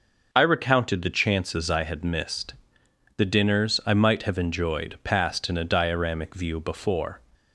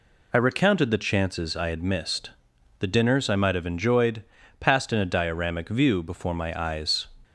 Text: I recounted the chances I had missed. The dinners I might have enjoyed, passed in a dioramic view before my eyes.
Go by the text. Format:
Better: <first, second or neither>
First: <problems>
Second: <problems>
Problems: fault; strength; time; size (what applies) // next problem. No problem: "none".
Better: second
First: stops before "my eyes"; at 7.3 s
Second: none